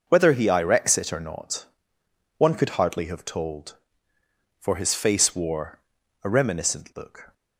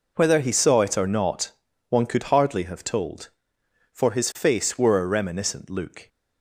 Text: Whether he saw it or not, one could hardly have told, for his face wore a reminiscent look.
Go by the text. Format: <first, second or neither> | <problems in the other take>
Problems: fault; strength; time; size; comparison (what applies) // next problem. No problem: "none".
second | says "irex" for "saw"; at 0.4 s // pauses between "wore" and "a"; at 5.7 s; 0.44 s long